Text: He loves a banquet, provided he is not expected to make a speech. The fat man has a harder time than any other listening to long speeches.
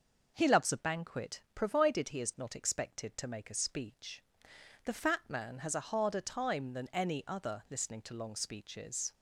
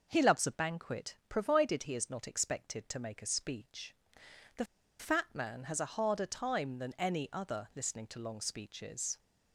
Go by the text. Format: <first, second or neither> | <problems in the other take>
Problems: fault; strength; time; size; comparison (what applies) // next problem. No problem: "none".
first | pauses between "The" and "fat"; slight; at 4.6 s; 0.34 s long